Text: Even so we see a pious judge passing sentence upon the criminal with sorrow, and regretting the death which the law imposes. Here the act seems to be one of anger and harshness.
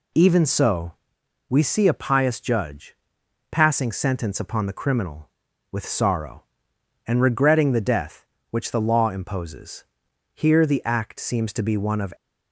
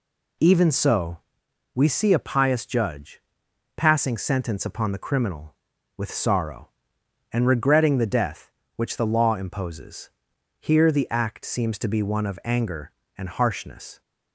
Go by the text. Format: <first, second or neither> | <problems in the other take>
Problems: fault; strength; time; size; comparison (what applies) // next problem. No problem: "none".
second | pauses between "so" and "we"; noticeable; at 0.9 s; 0.56 s long; noticeable in the second // pauses between "judge" and "passing"; noticeable; at 2.9 s; 0.52 s long; noticeable in the second // stops before "anger and harshness"; at 12.1 s